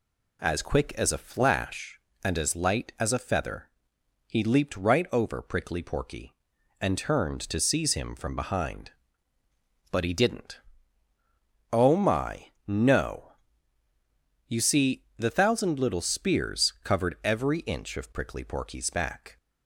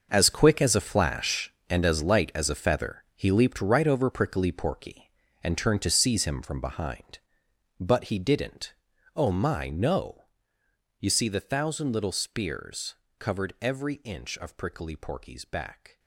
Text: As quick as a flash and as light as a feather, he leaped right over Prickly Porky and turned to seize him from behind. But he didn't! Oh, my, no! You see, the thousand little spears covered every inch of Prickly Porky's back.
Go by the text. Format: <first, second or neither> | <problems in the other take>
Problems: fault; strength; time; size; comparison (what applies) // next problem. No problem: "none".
first | gets quieter; strong; throughout; 13 dB // pauses between "spears" and "covered"; slight; at 12.9 s; 0.24 s long